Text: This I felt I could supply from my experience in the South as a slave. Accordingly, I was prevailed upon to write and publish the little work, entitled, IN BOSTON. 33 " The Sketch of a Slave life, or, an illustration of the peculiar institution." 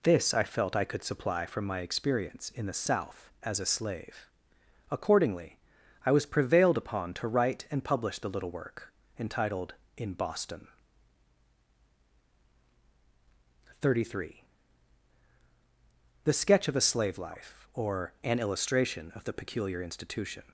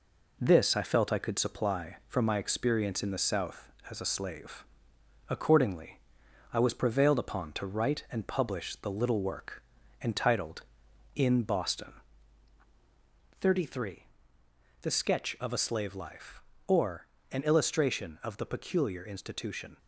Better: neither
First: none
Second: none

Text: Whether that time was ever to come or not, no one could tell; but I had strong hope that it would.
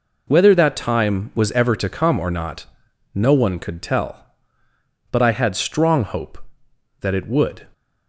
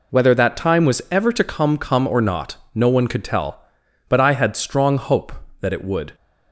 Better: first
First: none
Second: says "come" twice; at 1.7 s

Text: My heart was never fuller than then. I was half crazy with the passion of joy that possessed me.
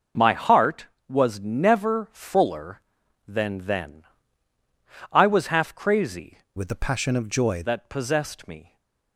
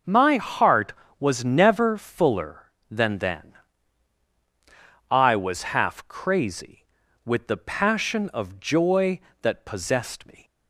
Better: second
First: changes voice from "with" to "joy"; from 6.5 to 7.6 s; 1.1 s long // stays silent after the last word; slight; from 8.6 s on; 0.5 s long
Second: none

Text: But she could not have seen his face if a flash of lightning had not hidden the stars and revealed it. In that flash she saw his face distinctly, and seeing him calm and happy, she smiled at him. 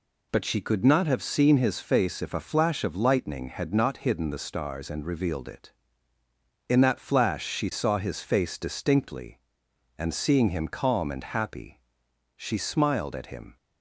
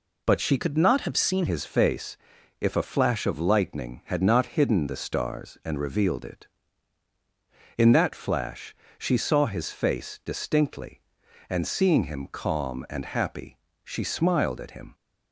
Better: first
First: none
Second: changes voice from "could" to "seen"; from 0.5 to 1.4 s; 0.9 s long // pauses between "face" and "if"; at 2.1 s; 0.42 s long // pauses between "flash" and "she"; slight; at 8.7 s; 0.22 s long

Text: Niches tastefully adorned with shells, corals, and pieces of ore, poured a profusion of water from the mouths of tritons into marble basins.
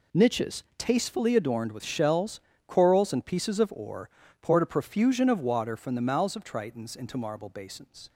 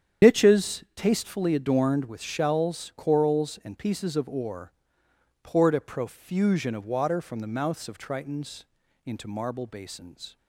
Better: first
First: none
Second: loses the start of "Niches"; at 0.2 s; 100 ms // starts louder than the rest; strong; until 1.3 s; 9 dB // pauses between "tritons" and "into"; at 8.6 s; 0.42 s long

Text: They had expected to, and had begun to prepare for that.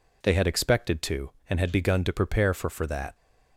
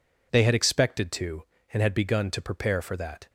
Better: second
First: says "for" twice; at 2.6 s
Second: none

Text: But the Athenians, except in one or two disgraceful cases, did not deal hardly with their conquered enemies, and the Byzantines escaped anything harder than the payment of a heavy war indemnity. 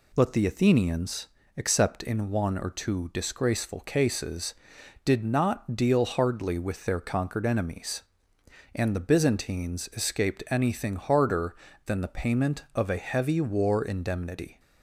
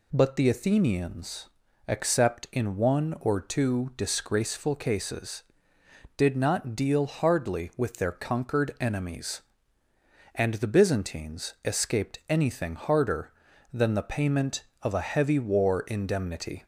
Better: neither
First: none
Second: none

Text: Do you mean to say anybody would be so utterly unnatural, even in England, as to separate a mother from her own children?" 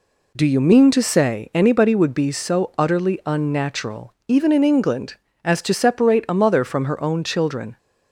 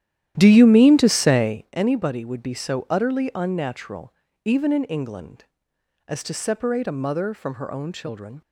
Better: first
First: none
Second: starts louder than the rest; strong; until 1.6 s; 12 dB

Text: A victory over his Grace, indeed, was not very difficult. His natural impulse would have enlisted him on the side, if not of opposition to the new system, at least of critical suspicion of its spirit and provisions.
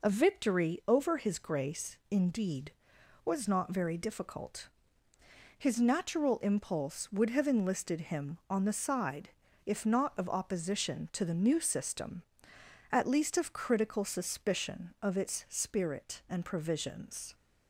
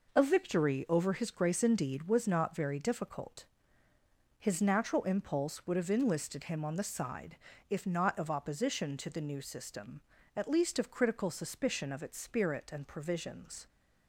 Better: neither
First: none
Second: none

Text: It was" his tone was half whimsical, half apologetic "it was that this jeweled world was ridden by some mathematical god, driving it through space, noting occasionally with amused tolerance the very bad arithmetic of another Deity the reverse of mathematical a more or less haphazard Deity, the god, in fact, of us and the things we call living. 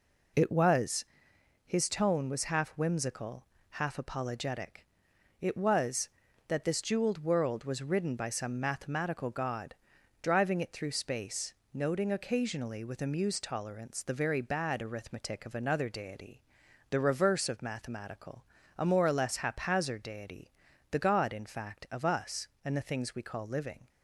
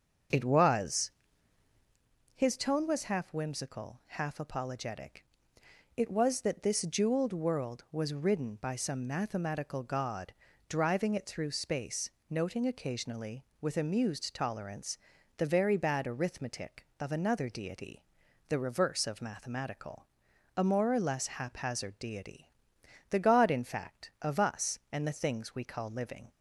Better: first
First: pauses between "was" and "his"; noticeable; at 1.0 s; 0.62 s long // pauses between "apologetic" and "it"; noticeable; at 4.8 s; 0.54 s long // pauses between "Deity" and "the"; noticeable; at 16.3 s; 0.50 s long // pauses between "mathematical" and "a"; slight; at 18.4 s; 0.32 s long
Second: starts louder than the rest; until 2.1 s; 7 dB // pauses between "was" and "his"; at 1.1 s; 1.2 s long // pauses between "apologetic" and "it"; noticeable; at 5.2 s; 0.72 s long // pauses between "tolerance" and "the"; at 14.9 s; 0.40 s long // pauses between "Deity" and "the"; noticeable; at 18.0 s; 0.46 s long // pauses between "mathematical" and "a"; noticeable; at 20.0 s; 0.50 s long

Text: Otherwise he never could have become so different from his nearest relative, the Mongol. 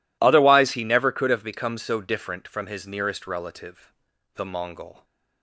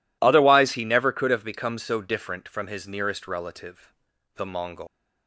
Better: first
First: none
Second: leaves "Mongol" unfinished; at 4.8 s; 170 ms

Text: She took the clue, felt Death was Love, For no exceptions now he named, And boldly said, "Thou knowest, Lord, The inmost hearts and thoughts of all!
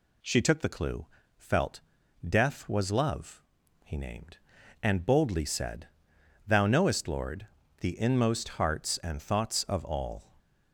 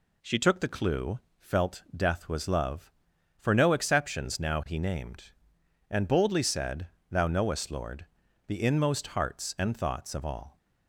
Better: second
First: pauses between "felt" and "Death"; noticeable; at 1.8 s; 0.46 s long // skips "For no exceptions now"; at 3.6 s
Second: none

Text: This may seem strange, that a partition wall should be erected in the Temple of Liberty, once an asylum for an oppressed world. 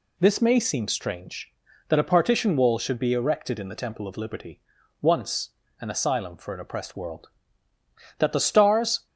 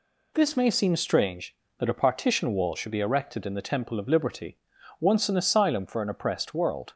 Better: second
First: pauses between "once" and "an"; slight; at 5.5 s; 0.30 s long // goes on to say "That the Stars"; noticeable; from 8.1 s on; 0.88 s long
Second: none

